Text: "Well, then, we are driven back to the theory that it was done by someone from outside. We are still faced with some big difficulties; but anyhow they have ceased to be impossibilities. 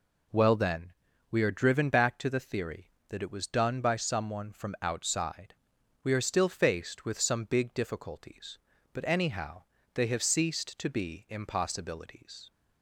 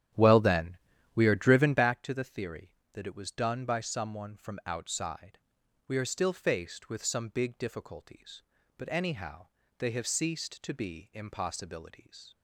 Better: first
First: pauses between "anyhow" and "they"; slight; at 9.6 s; 0.32 s long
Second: starts louder than the rest; strong; until 2.0 s; 11 dB // pauses between "anyhow" and "they"; slight; at 9.4 s; 0.32 s long

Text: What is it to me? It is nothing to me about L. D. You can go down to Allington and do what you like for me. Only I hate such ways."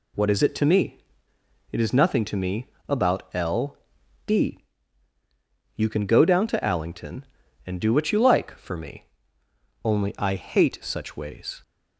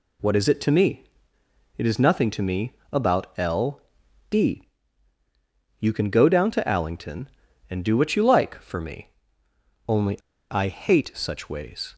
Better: first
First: pauses between "me" and "about"; slight; at 2.6 s; 0.22 s long // pauses between "L" and "D"; noticeable; at 3.7 s; 0.48 s long // pauses between "D" and "You"; at 4.5 s; 1.1 s long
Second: pauses between "me" and "about"; slight; at 2.7 s; 0.20 s long // pauses between "L" and "D"; noticeable; at 3.8 s; 0.48 s long // pauses between "D" and "You"; at 4.6 s; 1.1 s long // pauses between "Only" and "I"; slight; at 10.1 s; 0.31 s long

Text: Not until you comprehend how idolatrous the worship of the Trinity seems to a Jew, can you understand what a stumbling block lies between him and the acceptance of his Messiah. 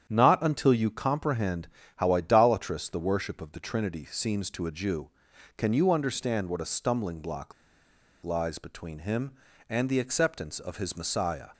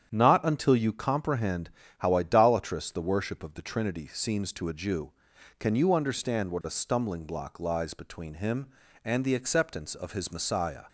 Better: second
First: starts louder than the rest; strong; until 1.1 s; 9 dB // pauses between "comprehend" and "how"; slight; at 1.6 s; 0.30 s long // pauses between "block" and "lies"; noticeable; at 7.5 s; 0.71 s long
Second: starts louder than the rest; strong; until 1.1 s; 9 dB // pauses between "comprehend" and "how"; slight; at 1.6 s; 0.30 s long

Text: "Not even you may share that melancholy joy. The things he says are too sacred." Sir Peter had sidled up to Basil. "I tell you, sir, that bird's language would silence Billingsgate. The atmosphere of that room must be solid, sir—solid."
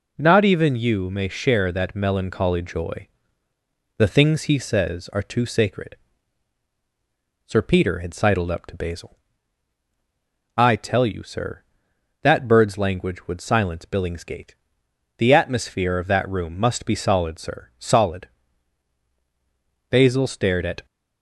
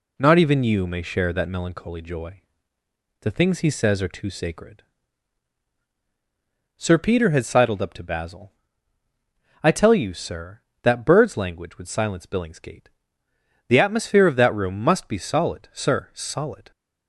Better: second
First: goes on to say "Basil stared at"; noticeable; from 19.8 s on; 0.96 s long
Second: none

